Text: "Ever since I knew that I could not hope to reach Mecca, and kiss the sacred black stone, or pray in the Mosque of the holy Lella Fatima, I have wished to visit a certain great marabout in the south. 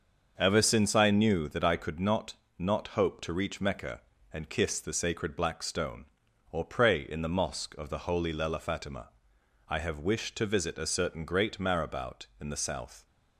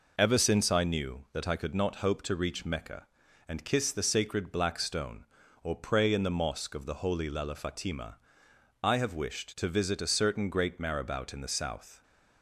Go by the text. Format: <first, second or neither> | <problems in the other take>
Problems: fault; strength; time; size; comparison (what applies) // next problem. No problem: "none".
second | starts louder than the rest; until 1.3 s; 6.5 dB // says "not" twice; at 2.5 s